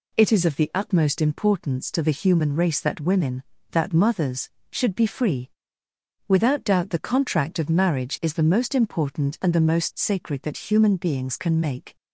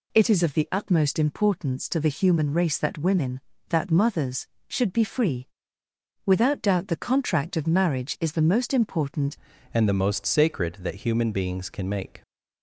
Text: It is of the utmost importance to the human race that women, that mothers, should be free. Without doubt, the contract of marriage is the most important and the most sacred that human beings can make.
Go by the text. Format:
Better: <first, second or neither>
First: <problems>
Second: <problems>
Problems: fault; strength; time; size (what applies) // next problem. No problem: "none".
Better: first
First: none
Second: changes voice at "and"; from 9.7 s on; 2.5 s long